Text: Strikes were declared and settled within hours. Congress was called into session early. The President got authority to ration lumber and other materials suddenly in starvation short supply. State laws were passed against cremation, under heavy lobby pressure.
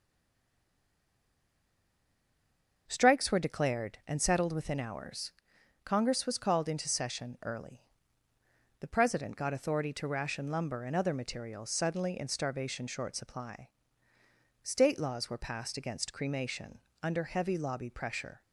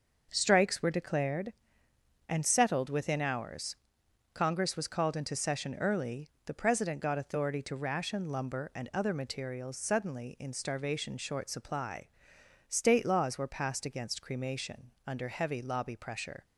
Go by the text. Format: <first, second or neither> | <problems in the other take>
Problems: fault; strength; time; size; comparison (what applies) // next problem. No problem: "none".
second | stays silent before the first word; strong; until 2.8 s; 2.8 s long // starts louder than the rest; until 3.8 s; 6 dB